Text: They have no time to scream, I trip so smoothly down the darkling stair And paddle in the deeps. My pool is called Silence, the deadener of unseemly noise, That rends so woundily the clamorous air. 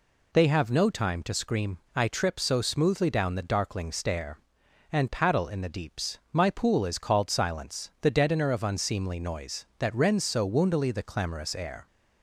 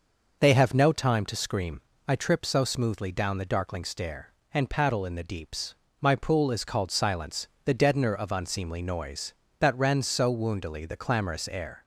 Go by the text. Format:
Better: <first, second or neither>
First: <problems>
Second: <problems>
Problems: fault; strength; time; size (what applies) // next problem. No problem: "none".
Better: neither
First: none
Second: none